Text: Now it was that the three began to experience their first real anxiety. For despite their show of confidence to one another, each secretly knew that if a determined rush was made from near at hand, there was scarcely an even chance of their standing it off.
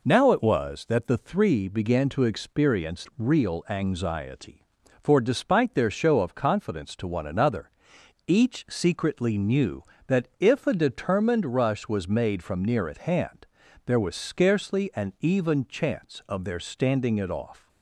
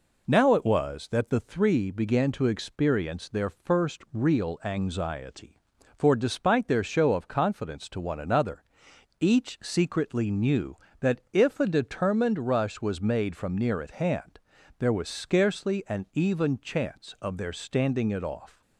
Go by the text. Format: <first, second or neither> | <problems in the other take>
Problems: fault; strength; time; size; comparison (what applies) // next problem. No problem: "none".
second | skips "their first"; at 3.1 s